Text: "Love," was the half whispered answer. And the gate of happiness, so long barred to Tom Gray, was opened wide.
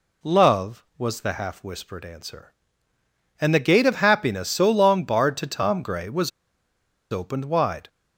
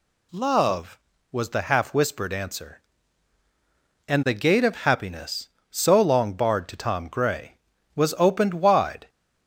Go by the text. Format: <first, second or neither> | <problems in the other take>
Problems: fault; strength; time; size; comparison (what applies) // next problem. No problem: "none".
second | pauses between "was" and "opened"; noticeable; at 6.2 s; 0.81 s long